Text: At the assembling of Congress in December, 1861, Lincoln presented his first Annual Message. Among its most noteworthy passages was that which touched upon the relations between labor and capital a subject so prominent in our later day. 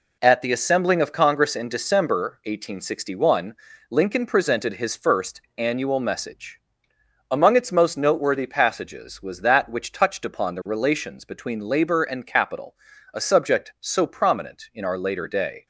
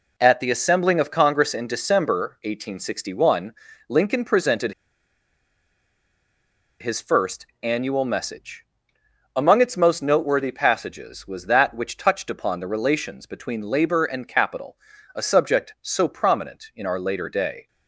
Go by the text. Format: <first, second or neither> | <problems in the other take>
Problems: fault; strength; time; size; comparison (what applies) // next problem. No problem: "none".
first | pauses between "presented" and "his"; strong; at 4.7 s; 2.0 s long // pauses between "first" and "Annual"; slight; at 7.4 s; 0.16 s long; slight in the first // pauses between "capital" and "a"; slight; at 14.7 s; 0.36 s long; slight in the first